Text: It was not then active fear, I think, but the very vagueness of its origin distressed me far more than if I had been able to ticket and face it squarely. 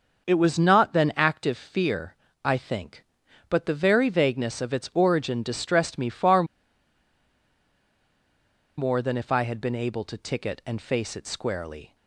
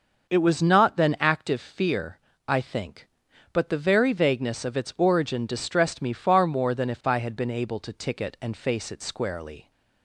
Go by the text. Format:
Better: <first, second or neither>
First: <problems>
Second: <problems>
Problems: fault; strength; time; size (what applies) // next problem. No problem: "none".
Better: second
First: starts louder than the rest; until 1.3 s; 6 dB // pauses between "far" and "more"; strong; at 6.4 s; 2.3 s long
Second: starts louder than the rest; until 1.3 s; 6.5 dB